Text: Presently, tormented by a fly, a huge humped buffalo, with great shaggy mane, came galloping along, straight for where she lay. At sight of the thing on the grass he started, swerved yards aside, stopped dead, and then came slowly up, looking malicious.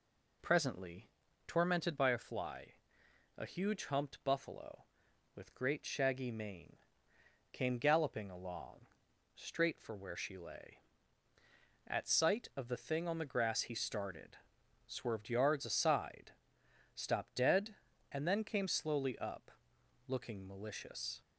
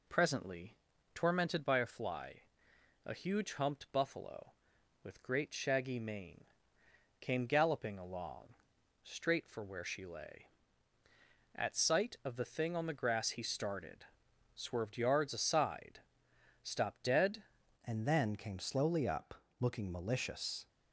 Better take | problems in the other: first | changes voice at "and"; from 17.8 s on; 2.8 s long

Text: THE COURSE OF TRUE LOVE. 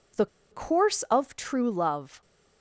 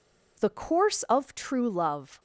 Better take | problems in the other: second | pauses between "THE" and "COURSE"; slight; at 0.2 s; 0.25 s long

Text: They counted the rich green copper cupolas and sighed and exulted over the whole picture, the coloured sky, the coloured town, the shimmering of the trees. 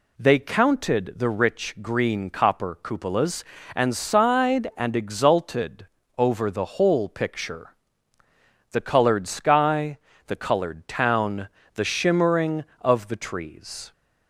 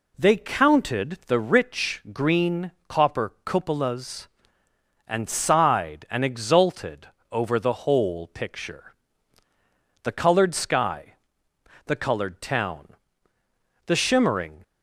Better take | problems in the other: first | pauses between "green" and "copper"; slight; at 2.7 s; 0.18 s long // pauses between "exulted" and "over"; slight; at 7.0 s; 0.24 s long; slight in the first // stops before "of the trees"; at 14.6 s

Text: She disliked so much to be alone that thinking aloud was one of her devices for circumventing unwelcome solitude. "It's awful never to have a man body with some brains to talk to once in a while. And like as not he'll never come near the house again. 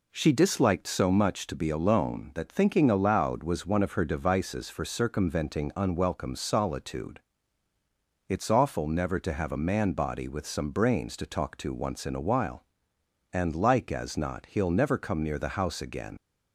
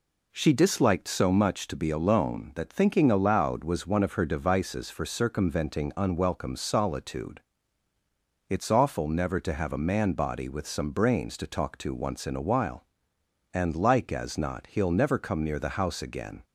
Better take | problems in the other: second | leaves "again" unfinished; at 16.1 s; 60 ms

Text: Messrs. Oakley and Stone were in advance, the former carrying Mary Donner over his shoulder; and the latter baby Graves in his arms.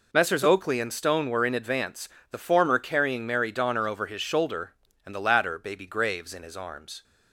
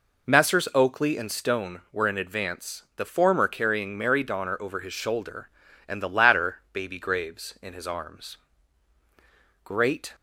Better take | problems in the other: first | goes on to say "Great"; from 9.6 s on; 0.50 s long

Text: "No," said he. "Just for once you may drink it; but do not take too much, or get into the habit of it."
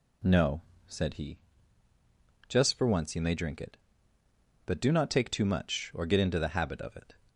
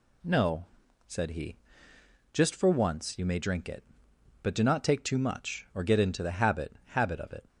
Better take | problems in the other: first | says "habit" twice; at 6.8 s

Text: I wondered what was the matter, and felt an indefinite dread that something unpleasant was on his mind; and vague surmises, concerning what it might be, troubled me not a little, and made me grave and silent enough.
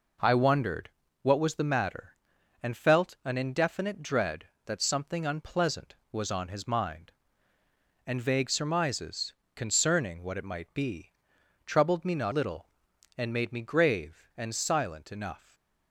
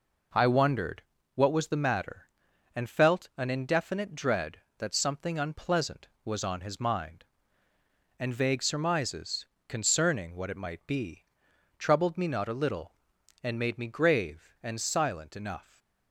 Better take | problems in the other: second | pauses between "wondered" and "what"; slight; at 0.8 s; 0.32 s long; slight in the second // skips "a"; at 12.3 s // stays silent after the last word; slight; from 15.3 s on; 0.6 s long

